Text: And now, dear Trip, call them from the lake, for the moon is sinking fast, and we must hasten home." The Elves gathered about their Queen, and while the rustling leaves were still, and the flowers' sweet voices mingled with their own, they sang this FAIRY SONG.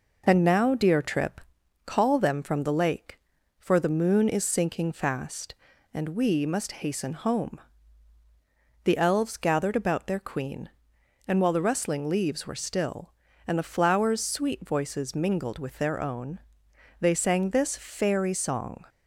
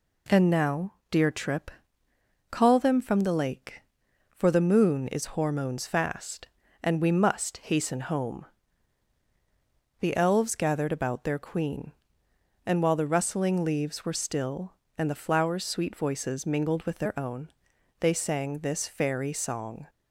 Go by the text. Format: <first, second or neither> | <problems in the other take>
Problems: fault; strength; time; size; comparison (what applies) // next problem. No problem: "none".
first | says "hormones" for "sinking"; at 5.3 s